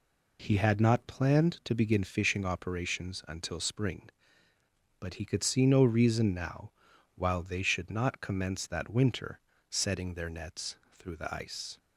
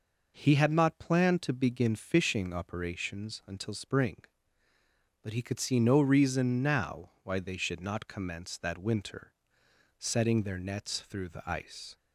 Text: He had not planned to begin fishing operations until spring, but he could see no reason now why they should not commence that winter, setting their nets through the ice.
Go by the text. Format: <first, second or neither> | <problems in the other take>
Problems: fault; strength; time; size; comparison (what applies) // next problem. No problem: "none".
second | says "while" for "why"; at 7.1 s // pauses between "nets" and "through"; slight; at 10.7 s; 0.16 s long